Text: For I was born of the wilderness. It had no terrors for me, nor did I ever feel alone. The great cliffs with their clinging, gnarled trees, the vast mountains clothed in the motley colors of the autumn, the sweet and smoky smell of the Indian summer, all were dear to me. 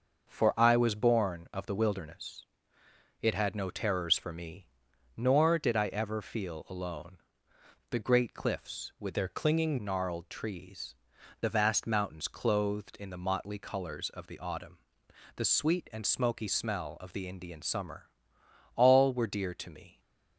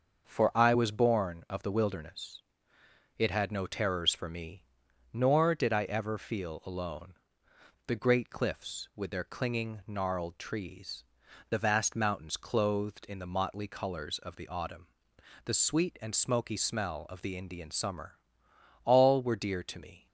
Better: second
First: starts louder than the rest; until 1.3 s; 6.5 dB // changes voice from "their" to "clinging"; from 9.1 to 9.7 s; 0.6 s long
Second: starts louder than the rest; until 1.3 s; 6.5 dB

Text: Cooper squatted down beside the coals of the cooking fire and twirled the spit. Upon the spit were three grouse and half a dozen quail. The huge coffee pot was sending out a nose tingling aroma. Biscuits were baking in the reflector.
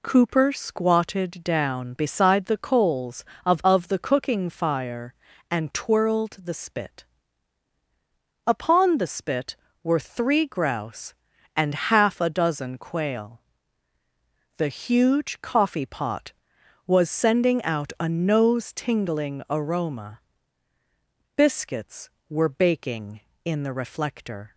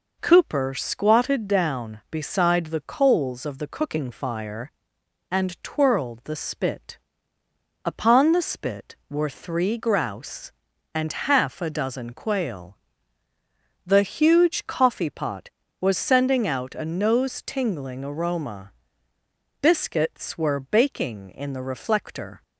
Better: second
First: says "of" twice; at 3.6 s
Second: none

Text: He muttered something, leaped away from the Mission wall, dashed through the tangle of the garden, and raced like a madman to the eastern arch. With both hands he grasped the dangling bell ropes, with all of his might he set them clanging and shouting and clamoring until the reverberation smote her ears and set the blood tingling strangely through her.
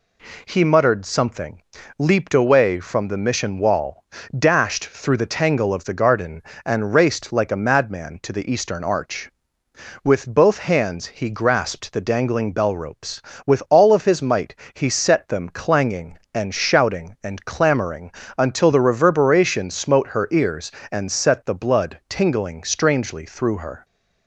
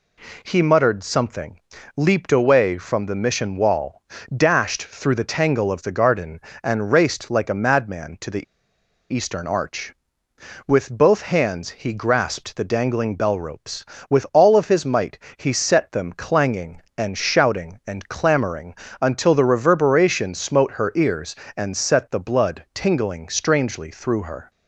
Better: first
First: pauses between "might" and "he"; slight; at 14.5 s; 0.20 s long // pauses between "clamoring" and "until"; slight; at 18.1 s; 0.26 s long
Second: pauses between "the" and "eastern"; noticeable; at 8.4 s; 0.65 s long // pauses between "might" and "he"; slight; at 15.1 s; 0.20 s long // pauses between "clamoring" and "until"; slight; at 18.7 s; 0.26 s long

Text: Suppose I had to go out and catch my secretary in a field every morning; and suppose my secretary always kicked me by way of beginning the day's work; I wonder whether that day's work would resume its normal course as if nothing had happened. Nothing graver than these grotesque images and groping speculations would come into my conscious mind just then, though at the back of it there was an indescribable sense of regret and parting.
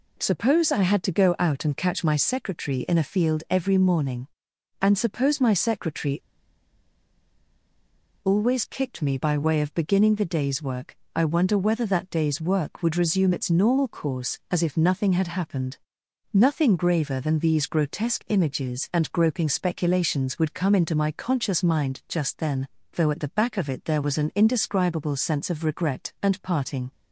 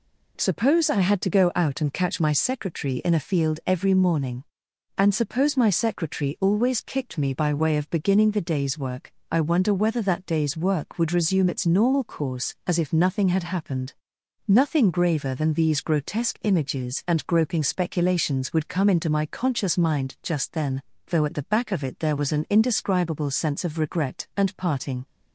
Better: second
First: pauses between "secretary" and "always"; strong; at 6.1 s; 2.0 s long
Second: none

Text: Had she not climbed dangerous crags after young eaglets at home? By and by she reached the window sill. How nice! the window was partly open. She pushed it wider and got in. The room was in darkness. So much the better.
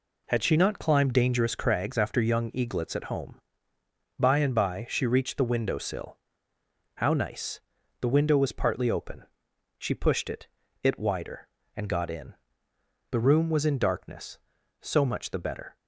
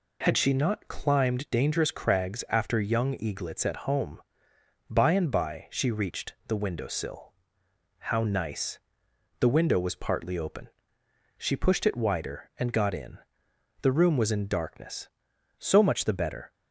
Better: second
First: says "it" twice; at 10.8 s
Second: none

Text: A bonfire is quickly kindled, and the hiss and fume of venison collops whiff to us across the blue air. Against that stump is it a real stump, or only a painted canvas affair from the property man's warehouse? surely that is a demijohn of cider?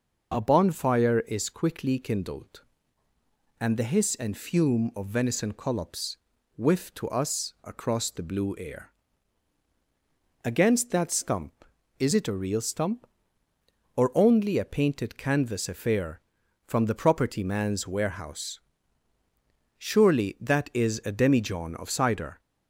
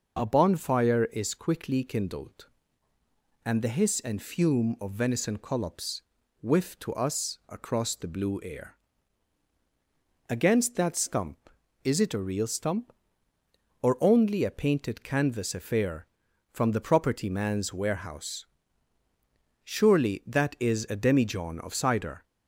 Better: neither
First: pauses between "collops" and "whiff"; at 6.1 s; 0.40 s long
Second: pauses between "collops" and "whiff"; at 6.0 s; 0.40 s long

